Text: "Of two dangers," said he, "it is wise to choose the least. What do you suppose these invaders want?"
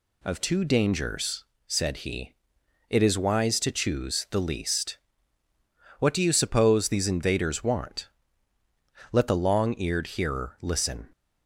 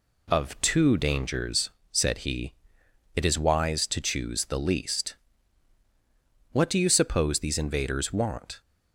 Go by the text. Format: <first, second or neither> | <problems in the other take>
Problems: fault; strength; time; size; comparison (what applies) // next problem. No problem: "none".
second | goes on to say "Let the Long Eared Hearer listen"; strong; from 9.1 s on; 1.9 s long